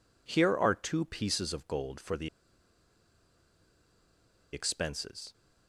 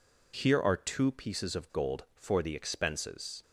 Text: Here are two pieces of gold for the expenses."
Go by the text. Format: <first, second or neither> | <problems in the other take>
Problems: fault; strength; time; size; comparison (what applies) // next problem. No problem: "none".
second | pauses between "the" and "expenses"; strong; at 2.2 s; 2.2 s long